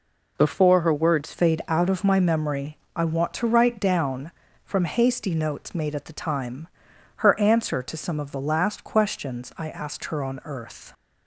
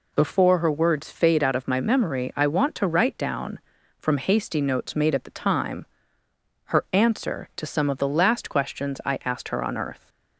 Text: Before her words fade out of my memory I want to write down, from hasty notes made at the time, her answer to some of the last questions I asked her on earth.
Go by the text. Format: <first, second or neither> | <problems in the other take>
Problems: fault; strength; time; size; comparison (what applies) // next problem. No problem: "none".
second | changes voice at "fade"; from 1.3 s on; 9.6 s long // pauses between "memory" and "I"; slight; at 2.7 s; 0.18 s long